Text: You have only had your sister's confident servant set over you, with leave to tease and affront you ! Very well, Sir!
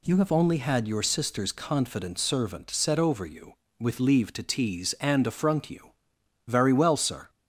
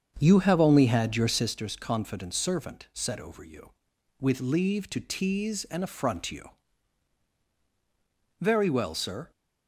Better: first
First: none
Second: starts louder than the rest; strong; until 1.5 s; 7 dB

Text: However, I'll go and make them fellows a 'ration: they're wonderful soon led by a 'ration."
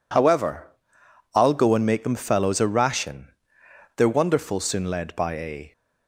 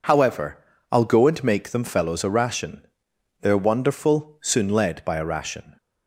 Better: second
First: stops before "ration"; at 5.7 s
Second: none

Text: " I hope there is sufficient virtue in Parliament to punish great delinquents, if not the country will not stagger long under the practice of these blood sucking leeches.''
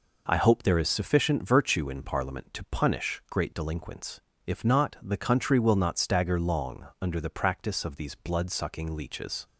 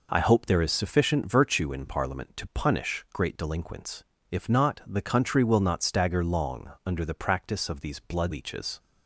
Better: first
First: none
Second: skips "sucking"; at 8.3 s

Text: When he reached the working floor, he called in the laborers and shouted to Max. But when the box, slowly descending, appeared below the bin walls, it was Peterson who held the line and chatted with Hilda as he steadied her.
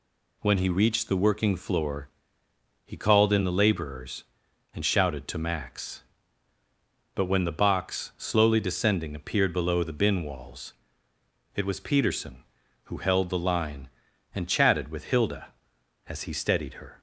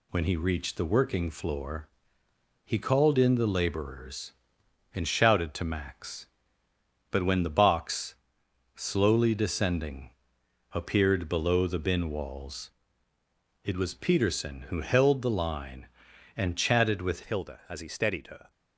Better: first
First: none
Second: changes voice at "Hilda"; from 17.2 s on; 1.2 s long

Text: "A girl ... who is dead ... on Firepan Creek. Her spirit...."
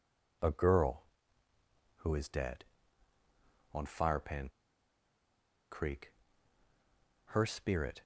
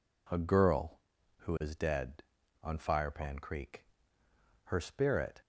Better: second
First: pauses between "Firepan" and "Creek"; at 4.4 s; 1.2 s long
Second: none

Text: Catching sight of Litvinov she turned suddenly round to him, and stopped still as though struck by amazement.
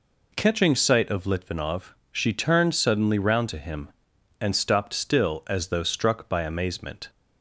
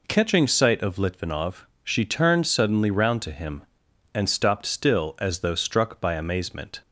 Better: neither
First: pauses between "Litvinov" and "she"; slight; at 1.9 s; 0.16 s long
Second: pauses between "Litvinov" and "she"; slight; at 1.6 s; 0.16 s long

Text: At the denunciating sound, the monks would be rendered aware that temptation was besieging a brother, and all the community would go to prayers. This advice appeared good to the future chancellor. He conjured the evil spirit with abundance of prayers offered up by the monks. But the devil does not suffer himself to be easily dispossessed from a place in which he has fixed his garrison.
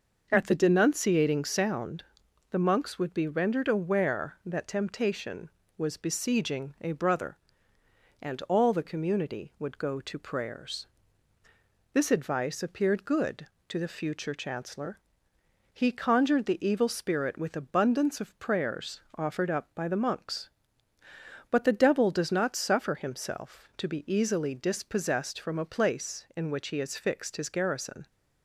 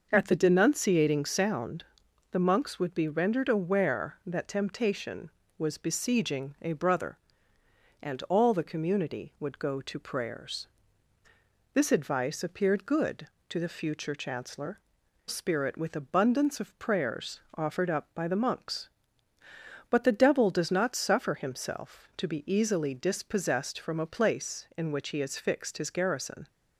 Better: first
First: pauses between "prayers" and "offered"; slight; at 18.9 s; 0.16 s long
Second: skips "He conjured the evil"; at 15.0 s // pauses between "prayers" and "offered"; slight; at 17.3 s; 0.16 s long

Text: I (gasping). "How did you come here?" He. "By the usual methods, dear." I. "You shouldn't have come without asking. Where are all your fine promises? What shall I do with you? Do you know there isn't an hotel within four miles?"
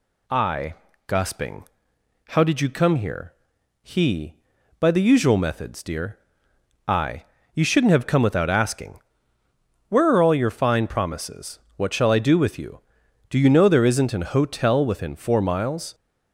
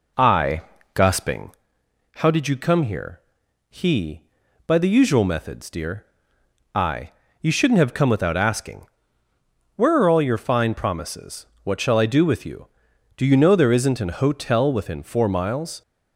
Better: first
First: none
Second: starts louder than the rest; noticeable; until 1.5 s; 4 dB

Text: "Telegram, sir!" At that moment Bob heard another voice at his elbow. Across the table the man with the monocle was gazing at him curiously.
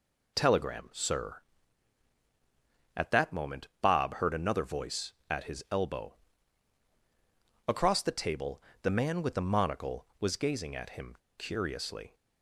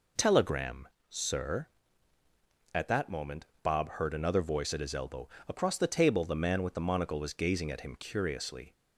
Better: second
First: pauses between "moment" and "Bob"; slight; at 3.6 s; 0.16 s long // pauses between "table" and "the"; slight; at 8.6 s; 0.22 s long // pauses between "him" and "curiously"; slight; at 11.1 s; 0.21 s long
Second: pauses between "moment" and "Bob"; slight; at 3.4 s; 0.20 s long

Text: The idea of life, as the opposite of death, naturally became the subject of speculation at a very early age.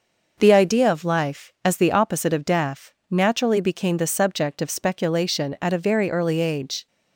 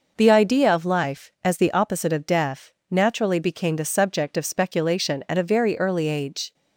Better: neither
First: none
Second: none

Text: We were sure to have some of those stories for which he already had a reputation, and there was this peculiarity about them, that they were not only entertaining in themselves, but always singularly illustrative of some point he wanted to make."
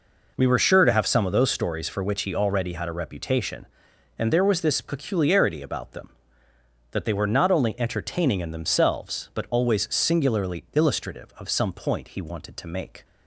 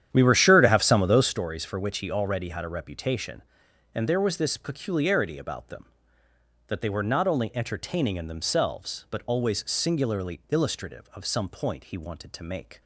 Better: first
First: none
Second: starts louder than the rest; strong; until 1.3 s; 10 dB

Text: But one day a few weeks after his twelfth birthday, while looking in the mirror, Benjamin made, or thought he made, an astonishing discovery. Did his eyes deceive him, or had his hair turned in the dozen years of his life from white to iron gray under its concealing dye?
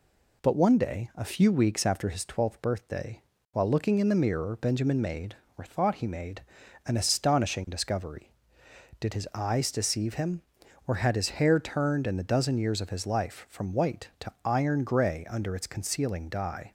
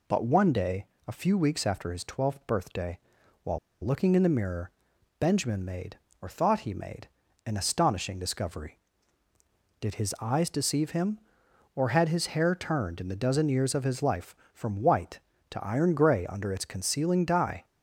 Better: first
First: none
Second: pauses between "day" and "a"; slight; at 0.8 s; 0.20 s long // pauses between "while" and "looking"; slight; at 3.5 s; 0.25 s long

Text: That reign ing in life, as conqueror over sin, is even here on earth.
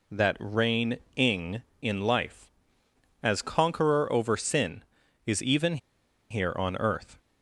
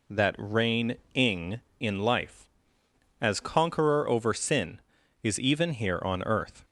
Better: second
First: pauses between "reign" and "ing"; slight; at 0.9 s; 0.18 s long // pauses between "even" and "here"; noticeable; at 5.7 s; 0.53 s long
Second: pauses between "reign" and "ing"; slight; at 0.9 s; 0.18 s long

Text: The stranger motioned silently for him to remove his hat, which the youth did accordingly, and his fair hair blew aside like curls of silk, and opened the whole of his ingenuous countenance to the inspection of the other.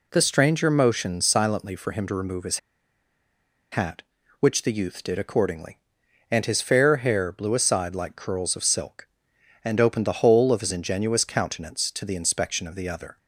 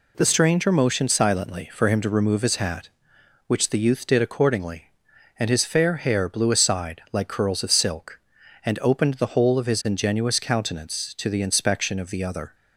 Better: second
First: pauses between "his" and "hat"; at 2.5 s; 1.1 s long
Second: none

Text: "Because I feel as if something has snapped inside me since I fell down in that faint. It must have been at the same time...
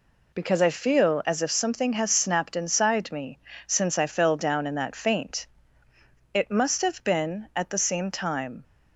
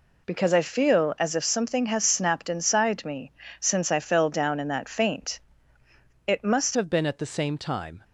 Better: first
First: pauses between "me" and "since"; slight; at 3.3 s; 0.30 s long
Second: pauses between "me" and "since"; slight; at 3.2 s; 0.30 s long // changes voice at "have"; from 6.7 s on; 1.3 s long

